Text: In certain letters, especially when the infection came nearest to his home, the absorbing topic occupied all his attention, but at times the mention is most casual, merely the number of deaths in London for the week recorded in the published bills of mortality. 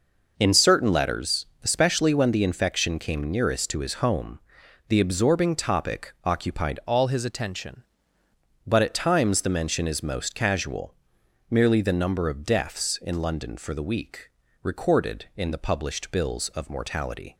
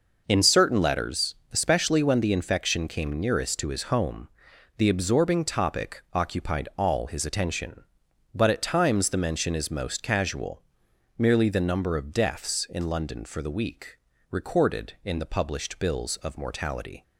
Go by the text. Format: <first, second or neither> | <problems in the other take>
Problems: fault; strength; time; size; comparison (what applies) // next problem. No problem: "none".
second | changes voice from "all" to "attention"; from 6.8 to 7.8 s; 1.0 s long // pauses between "week" and "recorded"; slight; at 14.2 s; 0.32 s long; slight in the second